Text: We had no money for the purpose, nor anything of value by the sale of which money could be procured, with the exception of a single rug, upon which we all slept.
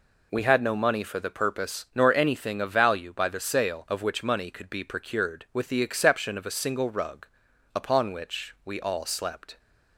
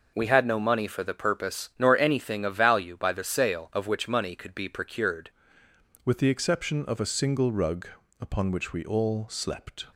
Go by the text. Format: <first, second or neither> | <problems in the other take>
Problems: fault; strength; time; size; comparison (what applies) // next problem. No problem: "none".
first | changes voice at "with"; from 6.0 s on; 3.8 s long